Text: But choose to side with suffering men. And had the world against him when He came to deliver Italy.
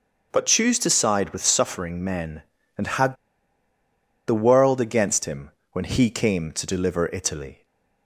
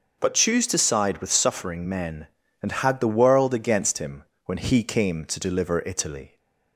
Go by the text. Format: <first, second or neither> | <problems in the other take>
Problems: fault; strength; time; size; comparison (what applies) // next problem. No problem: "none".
second | starts louder than the rest; noticeable; until 1.3 s; 6 dB; noticeable in the second // pauses between "had" and "the"; at 3.1 s; 1.1 s long // pauses between "him" and "when"; slight; at 5.5 s; 0.22 s long; slight in the second // stays silent after the last word; slight; from 7.5 s on; 0.5 s long